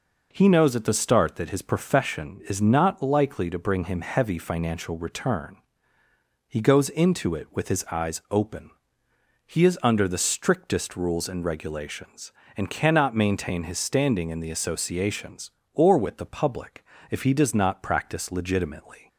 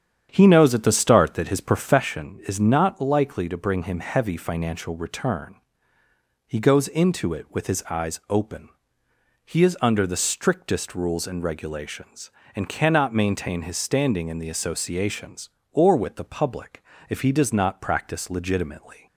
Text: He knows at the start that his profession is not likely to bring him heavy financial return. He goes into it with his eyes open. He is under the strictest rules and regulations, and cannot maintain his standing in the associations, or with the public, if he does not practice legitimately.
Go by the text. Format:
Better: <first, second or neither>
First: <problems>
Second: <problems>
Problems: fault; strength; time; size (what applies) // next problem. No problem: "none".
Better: first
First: none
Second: starts louder than the rest; strong; until 2.1 s; 8.5 dB